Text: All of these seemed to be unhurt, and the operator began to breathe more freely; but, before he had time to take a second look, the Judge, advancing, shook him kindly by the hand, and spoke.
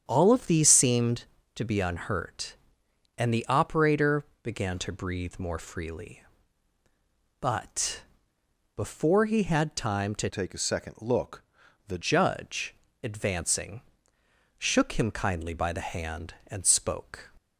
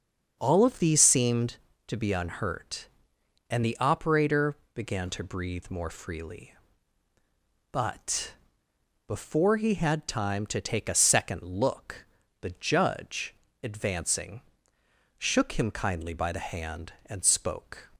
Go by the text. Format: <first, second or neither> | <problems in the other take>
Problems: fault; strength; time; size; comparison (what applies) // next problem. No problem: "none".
second | starts louder than the rest; strong; until 1.0 s; 8 dB; also in the second // pauses between "operator" and "began"; slight; at 4.2 s; 0.18 s long; slight in the second // changes voice from "take" to "the"; from 10.2 to 11.9 s; 1.7 s long